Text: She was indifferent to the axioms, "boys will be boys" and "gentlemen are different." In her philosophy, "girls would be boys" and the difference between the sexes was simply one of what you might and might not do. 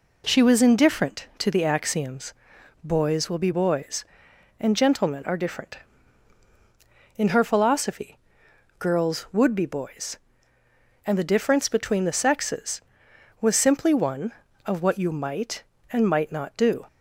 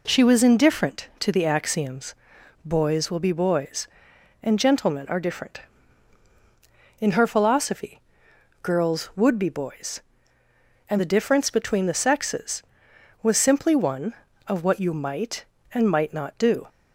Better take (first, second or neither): neither